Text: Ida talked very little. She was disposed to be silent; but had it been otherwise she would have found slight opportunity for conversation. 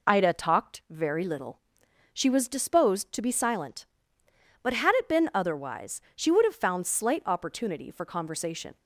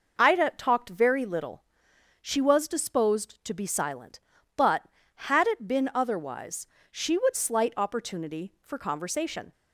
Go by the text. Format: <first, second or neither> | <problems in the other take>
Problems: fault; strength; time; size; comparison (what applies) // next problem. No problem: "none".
first | pauses between "otherwise" and "she"; slight; at 6.6 s; 0.24 s long; slight in the first // skips "have found"; at 7.3 s